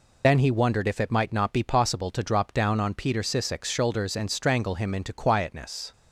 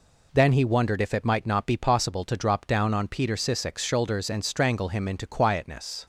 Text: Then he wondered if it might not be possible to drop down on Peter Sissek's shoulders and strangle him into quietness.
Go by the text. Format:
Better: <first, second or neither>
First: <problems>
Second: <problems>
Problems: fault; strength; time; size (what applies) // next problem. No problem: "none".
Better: second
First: loses the start of "Then"; at 0.2 s; 70 ms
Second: none